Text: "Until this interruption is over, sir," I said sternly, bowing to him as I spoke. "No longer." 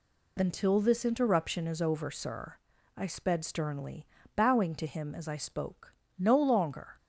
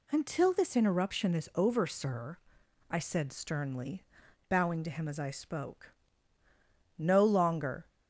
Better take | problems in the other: second | says "sped" for "said"; at 3.0 s

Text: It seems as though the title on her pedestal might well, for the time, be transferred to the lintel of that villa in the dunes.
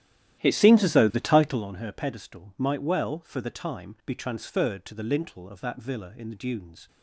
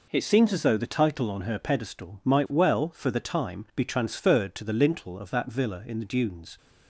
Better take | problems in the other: second | starts louder than the rest; strong; until 1.7 s; 12.5 dB

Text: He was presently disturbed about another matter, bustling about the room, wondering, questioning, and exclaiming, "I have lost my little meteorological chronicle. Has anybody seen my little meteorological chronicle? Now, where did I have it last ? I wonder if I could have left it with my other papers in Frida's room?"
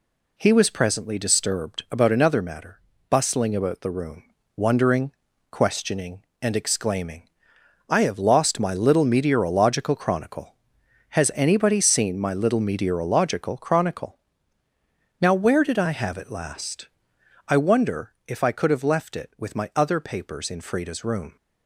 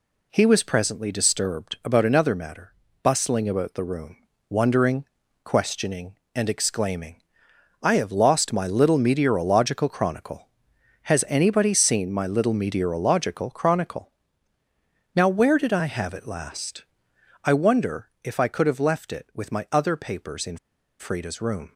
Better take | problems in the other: first | pauses between "in" and "Frida's"; at 20.5 s; 0.41 s long

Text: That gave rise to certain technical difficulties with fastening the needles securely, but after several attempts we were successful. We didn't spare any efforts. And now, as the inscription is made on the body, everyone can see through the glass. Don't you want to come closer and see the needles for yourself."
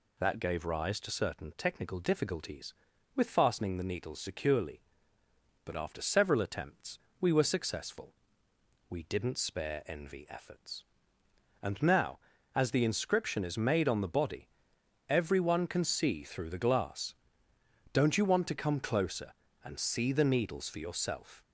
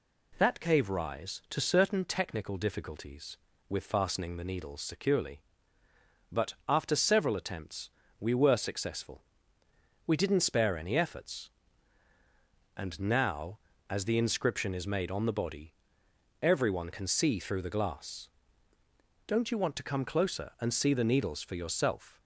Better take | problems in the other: second | pauses between "attempts" and "we"; slight; at 6.9 s; 0.22 s long; slight in the second // says "envy" for "any"; at 9.8 s

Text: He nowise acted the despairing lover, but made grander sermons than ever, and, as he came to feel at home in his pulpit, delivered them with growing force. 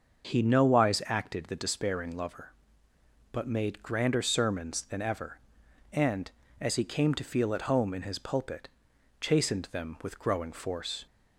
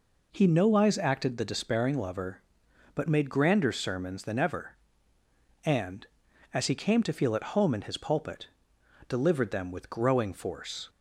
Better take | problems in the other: second | starts louder than the rest; until 1.3 s; 6 dB // says "chastened" for "delivered"; at 9.1 s

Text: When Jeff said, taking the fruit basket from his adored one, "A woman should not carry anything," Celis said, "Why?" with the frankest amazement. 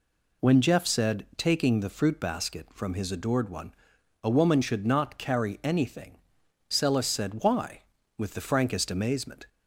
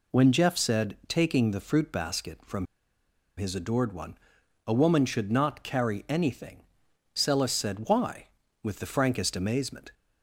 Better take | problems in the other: first | pauses between "from" and "his"; noticeable; at 2.6 s; 0.71 s long

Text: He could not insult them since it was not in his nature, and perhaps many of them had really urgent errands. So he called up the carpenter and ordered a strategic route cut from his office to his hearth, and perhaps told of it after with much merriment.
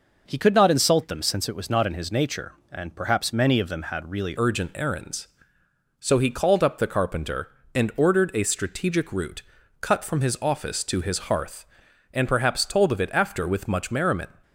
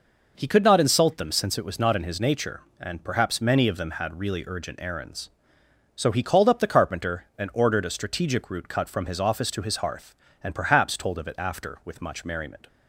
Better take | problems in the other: second | changes voice at "urgent"; from 4.3 s on; 9.9 s long // pauses between "route" and "cut"; at 9.4 s; 0.38 s long

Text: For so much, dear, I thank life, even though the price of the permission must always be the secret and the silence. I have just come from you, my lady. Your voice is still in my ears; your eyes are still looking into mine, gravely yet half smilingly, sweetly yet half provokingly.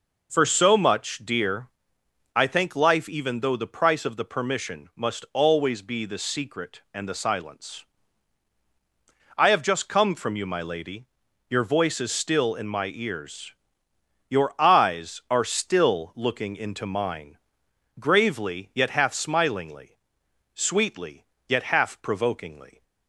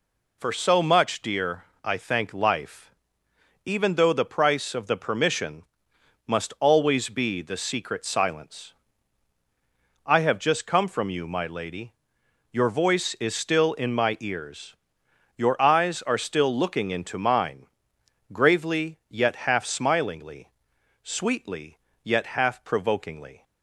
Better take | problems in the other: first | pauses between "permission" and "must"; noticeable; at 5.6 s; 0.64 s long // skips "and the"; at 8.0 s // pauses between "sweetly" and "yet"; slight; at 21.7 s; 0.22 s long; slight in the first

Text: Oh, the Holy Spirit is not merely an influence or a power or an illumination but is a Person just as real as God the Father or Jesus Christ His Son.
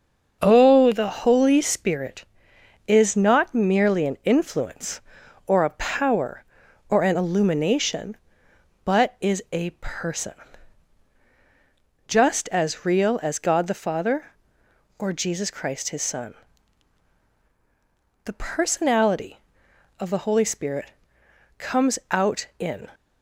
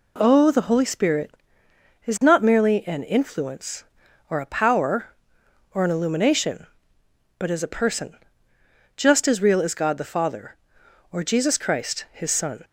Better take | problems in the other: second | starts louder than the rest; until 1.4 s; 6 dB // pauses between "Person" and "just"; strong; at 10.3 s; 1.7 s long; noticeable in the second // goes on to say "The personality of the Holy Spirit comes out in"; strong; from 18.2 s on; 4.6 s long

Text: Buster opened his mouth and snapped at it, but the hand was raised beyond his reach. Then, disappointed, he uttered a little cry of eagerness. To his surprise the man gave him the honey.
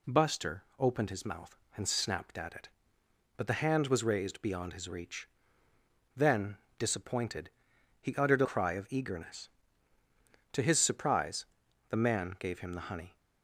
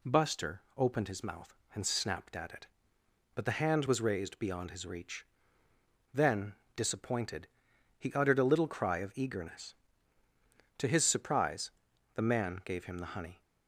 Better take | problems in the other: second | skips "little"; at 8.4 s // pauses between "surprise" and "the"; noticeable; at 11.4 s; 0.46 s long; noticeable in the second

